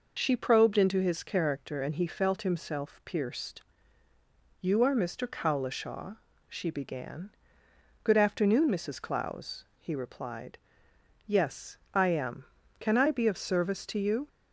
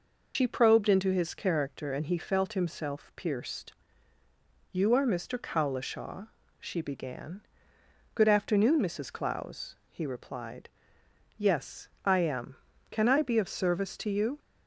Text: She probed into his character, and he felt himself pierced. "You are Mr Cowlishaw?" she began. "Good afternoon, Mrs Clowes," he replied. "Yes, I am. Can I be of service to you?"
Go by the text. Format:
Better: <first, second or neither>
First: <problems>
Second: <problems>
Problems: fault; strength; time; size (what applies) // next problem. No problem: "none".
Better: first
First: none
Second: loses the start of "She"; at 0.3 s; 75 ms